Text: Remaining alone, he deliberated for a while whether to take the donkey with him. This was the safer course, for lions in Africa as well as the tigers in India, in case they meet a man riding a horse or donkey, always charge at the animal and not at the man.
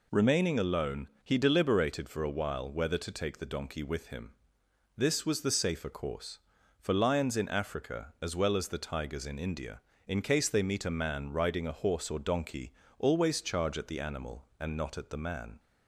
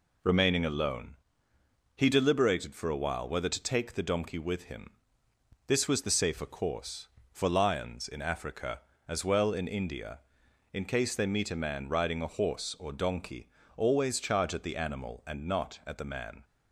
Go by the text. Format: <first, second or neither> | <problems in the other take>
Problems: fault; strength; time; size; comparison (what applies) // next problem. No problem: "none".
first | skips "as the tigers"; at 9.5 s